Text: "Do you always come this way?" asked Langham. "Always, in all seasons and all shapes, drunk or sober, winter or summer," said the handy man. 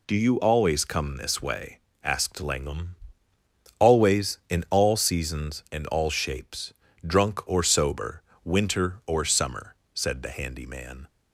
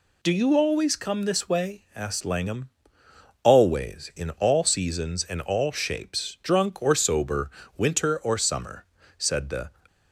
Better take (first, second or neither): first